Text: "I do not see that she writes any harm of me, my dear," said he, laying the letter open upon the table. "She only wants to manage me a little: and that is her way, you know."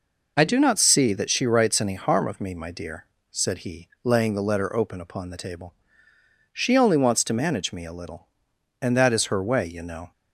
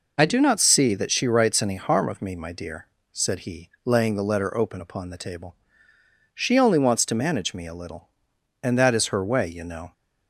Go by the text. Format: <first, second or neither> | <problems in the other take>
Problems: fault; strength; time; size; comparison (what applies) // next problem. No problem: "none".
neither | none